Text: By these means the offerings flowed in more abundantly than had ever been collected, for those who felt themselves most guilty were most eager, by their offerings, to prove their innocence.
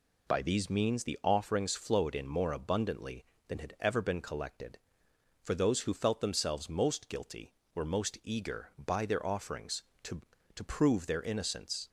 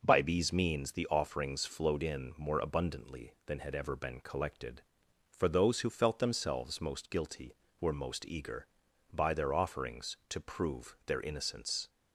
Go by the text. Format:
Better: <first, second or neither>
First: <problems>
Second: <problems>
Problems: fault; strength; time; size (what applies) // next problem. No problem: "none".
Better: second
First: says "to" twice; at 10.5 s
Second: none